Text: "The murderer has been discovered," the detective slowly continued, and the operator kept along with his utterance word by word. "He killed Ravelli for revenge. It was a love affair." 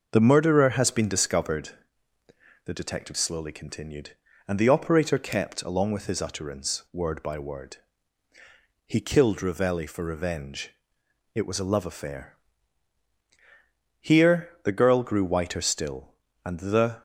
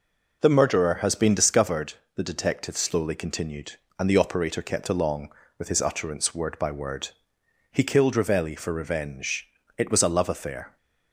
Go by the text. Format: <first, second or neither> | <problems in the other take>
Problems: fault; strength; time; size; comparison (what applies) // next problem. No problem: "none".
second | goes on to say "Here the girl grew whiter still and the"; strong; from 13.9 s on; 3.0 s long